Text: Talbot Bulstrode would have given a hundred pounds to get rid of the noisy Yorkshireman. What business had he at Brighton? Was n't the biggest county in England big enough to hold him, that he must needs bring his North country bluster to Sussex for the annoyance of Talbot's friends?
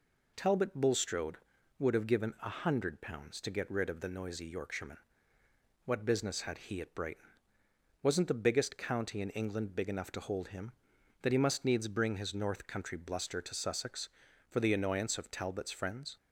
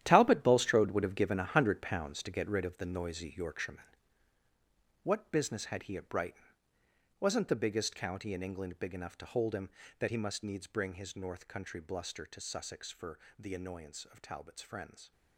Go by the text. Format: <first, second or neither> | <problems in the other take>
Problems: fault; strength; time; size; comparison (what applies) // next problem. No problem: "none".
first | gets quieter; strong; throughout; 12.5 dB // pauses between "for" and "the"; slight; at 13.1 s; 0.18 s long